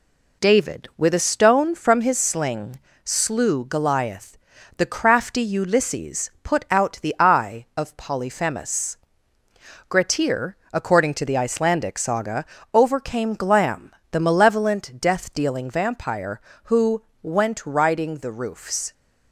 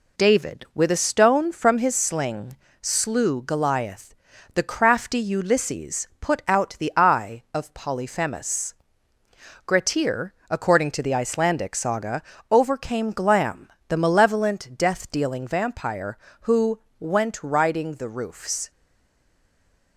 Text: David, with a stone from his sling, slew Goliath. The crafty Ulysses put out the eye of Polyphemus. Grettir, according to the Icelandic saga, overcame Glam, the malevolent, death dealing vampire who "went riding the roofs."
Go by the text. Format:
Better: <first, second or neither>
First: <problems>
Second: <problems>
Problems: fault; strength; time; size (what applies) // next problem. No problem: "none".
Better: first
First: pauses between "who" and "went"; slight; at 17.0 s; 0.18 s long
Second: pauses between "who" and "went"; slight; at 16.7 s; 0.18 s long // stays silent after the last word; noticeable; from 18.6 s on; 1.3 s long